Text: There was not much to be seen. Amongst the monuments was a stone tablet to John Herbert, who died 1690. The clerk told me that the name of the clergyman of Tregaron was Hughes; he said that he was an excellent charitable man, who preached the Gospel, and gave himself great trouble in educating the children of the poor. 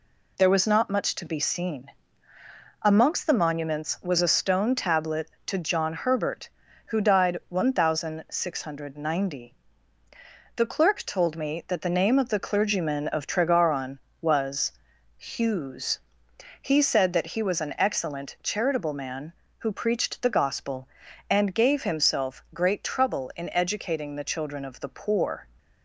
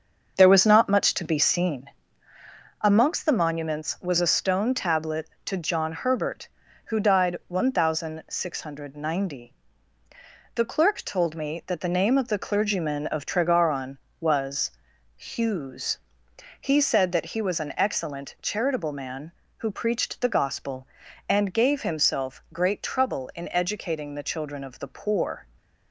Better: first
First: pauses between "was" and "Hughes"; noticeable; at 14.7 s; 0.46 s long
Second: starts louder than the rest; until 2.0 s; 6.5 dB // pauses between "was" and "Hughes"; noticeable; at 14.7 s; 0.46 s long

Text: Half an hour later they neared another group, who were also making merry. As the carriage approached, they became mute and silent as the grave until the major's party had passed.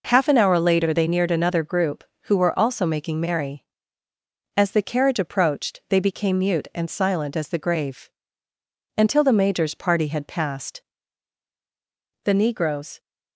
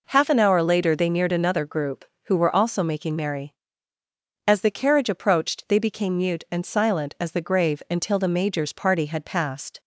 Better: second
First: pauses between "grave" and "until"; noticeable; at 8.1 s; 0.84 s long // goes on to say "The negroes"; noticeable; from 12.2 s on; 0.76 s long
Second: none

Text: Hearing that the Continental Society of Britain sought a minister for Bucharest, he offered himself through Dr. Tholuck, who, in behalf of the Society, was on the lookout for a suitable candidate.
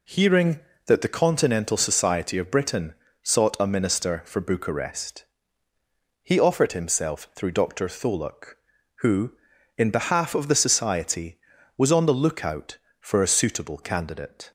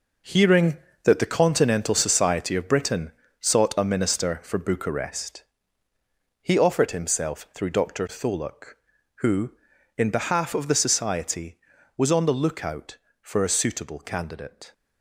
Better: first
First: pauses between "Britain" and "sought"; slight; at 2.9 s; 0.30 s long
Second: gets quieter; strong; throughout; 10.5 dB // pauses between "Britain" and "sought"; slight; at 3.1 s; 0.30 s long

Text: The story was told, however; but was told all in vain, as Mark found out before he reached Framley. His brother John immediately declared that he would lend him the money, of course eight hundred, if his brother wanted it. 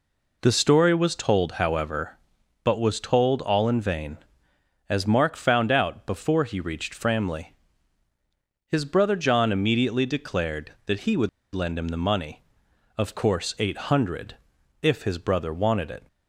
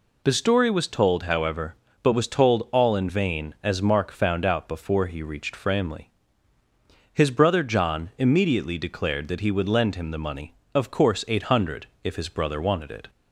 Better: second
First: pauses between "would" and "lend"; slight; at 11.2 s; 0.25 s long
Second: none

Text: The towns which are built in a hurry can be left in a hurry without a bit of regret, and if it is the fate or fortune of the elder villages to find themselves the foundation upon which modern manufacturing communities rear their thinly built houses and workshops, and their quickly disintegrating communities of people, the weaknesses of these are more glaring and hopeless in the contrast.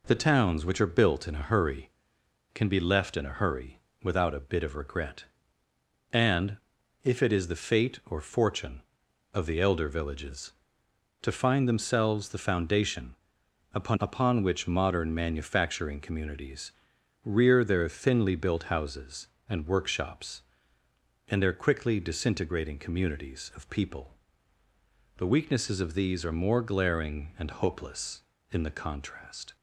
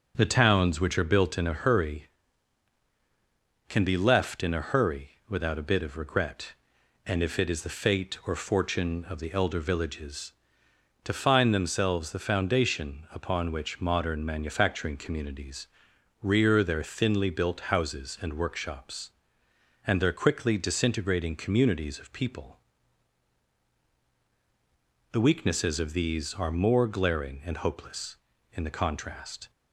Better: second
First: pauses between "hurry" and "without"; slight; at 3.7 s; 0.24 s long // pauses between "and" and "if"; noticeable; at 6.5 s; 0.46 s long // pauses between "foundation" and "upon"; noticeable; at 13.1 s; 0.58 s long // says "upon" twice; at 13.9 s // pauses between "communities" and "rear"; noticeable; at 16.7 s; 0.52 s long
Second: pauses between "hurry" and "without"; slight; at 5.0 s; 0.18 s long // pauses between "communities" and "rear"; noticeable; at 15.6 s; 0.56 s long

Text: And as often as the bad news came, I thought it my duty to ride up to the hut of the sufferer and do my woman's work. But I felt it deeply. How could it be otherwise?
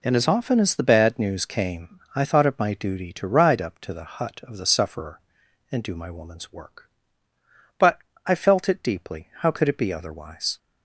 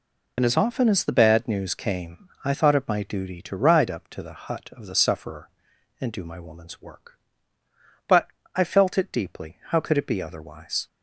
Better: first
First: pauses between "But" and "I"; slight; at 7.9 s; 0.28 s long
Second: loses the start of "And"; at 0.3 s; 50 ms // pauses between "But" and "I"; slight; at 8.2 s; 0.28 s long

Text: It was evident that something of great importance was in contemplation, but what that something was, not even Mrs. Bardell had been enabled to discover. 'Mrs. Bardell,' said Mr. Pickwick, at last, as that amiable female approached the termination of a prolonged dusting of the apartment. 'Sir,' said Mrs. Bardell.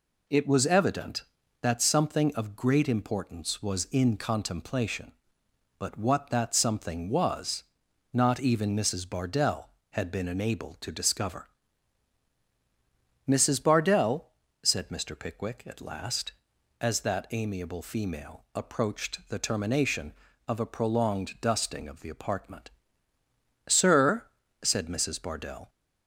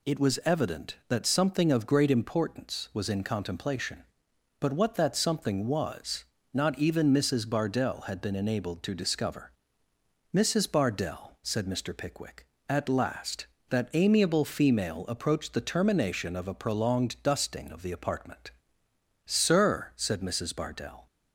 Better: first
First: none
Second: skips "as"; at 13.5 s

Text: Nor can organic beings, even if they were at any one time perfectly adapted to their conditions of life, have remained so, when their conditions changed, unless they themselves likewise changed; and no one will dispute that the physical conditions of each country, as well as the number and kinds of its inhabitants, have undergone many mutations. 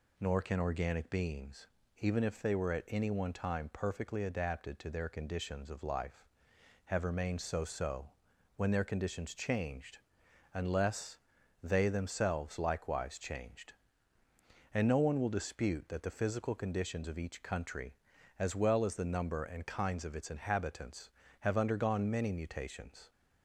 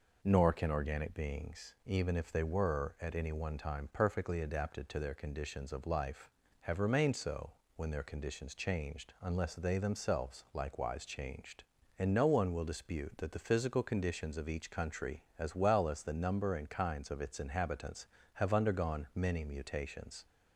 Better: second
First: says "so" twice; at 7.6 s // pauses between "unless" and "they"; at 11.1 s; 0.44 s long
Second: none

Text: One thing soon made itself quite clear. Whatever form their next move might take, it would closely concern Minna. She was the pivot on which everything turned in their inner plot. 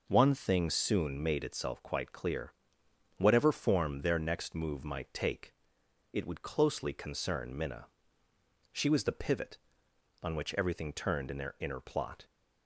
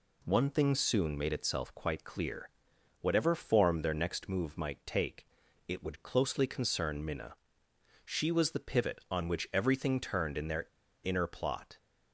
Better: first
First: none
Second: pauses between "their" and "inner"; at 10.6 s; 0.40 s long

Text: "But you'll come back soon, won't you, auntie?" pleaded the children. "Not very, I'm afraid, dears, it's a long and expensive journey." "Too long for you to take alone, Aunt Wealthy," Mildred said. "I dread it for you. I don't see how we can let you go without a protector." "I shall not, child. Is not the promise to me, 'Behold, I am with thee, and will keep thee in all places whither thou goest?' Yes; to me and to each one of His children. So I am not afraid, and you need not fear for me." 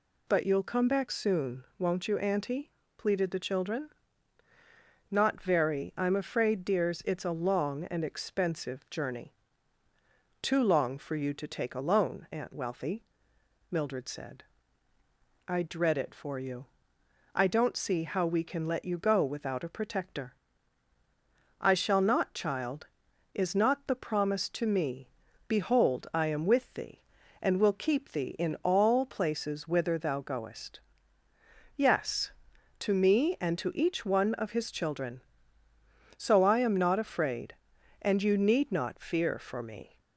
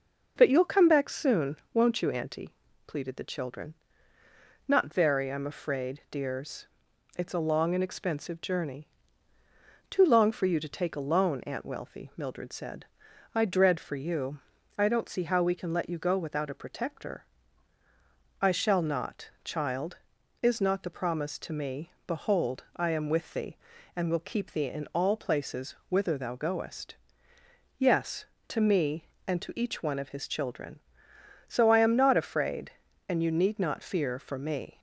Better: first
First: none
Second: skips "it"; at 13.7 s

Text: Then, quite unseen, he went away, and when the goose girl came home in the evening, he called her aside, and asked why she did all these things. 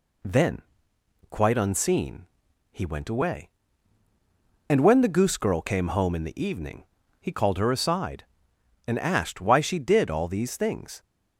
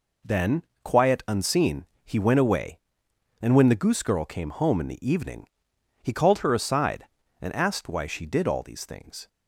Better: first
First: none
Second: says "quiet" for "quite"; at 0.8 s

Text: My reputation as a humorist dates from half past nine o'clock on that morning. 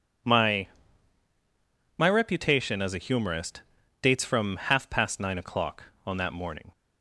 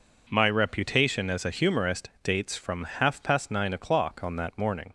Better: second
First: says "My" twice; at 1.9 s // pauses between "humorist" and "dates"; at 3.6 s; 0.42 s long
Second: pauses between "humorist" and "dates"; slight; at 2.0 s; 0.16 s long

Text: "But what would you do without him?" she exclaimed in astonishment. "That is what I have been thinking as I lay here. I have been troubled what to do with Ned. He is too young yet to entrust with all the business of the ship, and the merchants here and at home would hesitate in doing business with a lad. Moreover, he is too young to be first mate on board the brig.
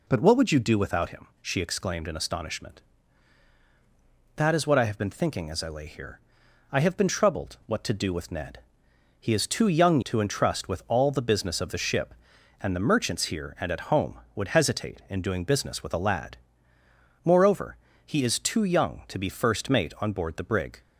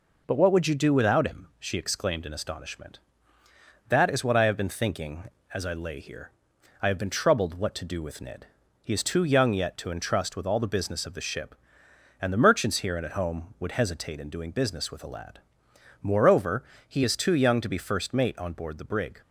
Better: second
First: skips "yet"; at 10.0 s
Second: none

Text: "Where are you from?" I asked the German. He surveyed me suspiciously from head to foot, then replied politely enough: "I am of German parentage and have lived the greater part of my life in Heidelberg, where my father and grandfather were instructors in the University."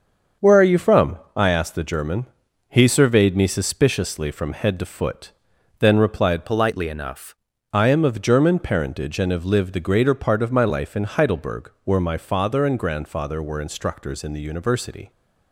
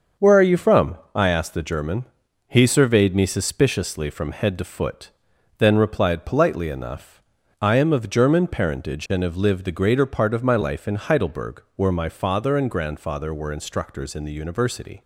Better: second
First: starts louder than the rest; until 1.5 s; 7 dB // changes voice from "politely" to "enough"; from 6.4 to 7.3 s; 0.9 s long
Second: starts louder than the rest; until 1.3 s; 6.5 dB

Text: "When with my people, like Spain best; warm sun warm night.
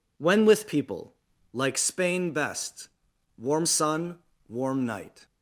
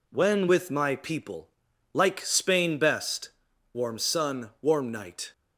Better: second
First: skips "my"; at 0.6 s // pauses between "sun" and "warm"; slight; at 4.1 s; 0.30 s long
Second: none

